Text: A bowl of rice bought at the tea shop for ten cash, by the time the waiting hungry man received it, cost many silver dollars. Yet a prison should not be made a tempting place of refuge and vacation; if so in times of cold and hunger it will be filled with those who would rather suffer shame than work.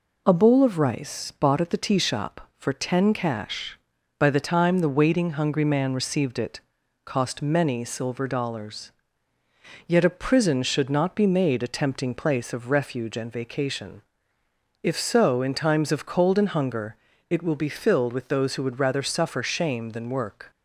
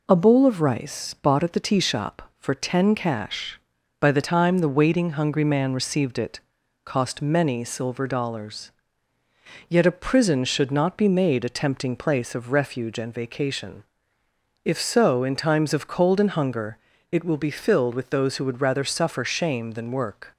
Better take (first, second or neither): neither